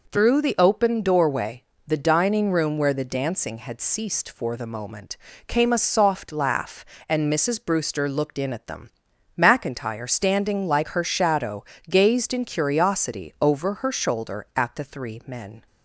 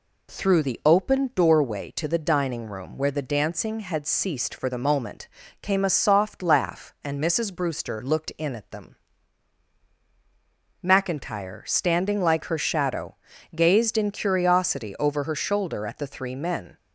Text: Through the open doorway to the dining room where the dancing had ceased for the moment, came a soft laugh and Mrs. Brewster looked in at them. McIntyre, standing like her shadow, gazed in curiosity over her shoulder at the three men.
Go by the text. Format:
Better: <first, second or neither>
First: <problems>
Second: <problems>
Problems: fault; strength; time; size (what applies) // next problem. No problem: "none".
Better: second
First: skips "to"; at 1.7 s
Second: none